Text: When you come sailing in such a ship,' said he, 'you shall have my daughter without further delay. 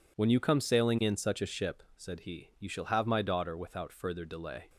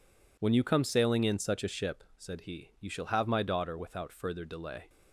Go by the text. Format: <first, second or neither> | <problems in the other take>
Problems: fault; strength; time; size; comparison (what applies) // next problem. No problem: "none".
neither | none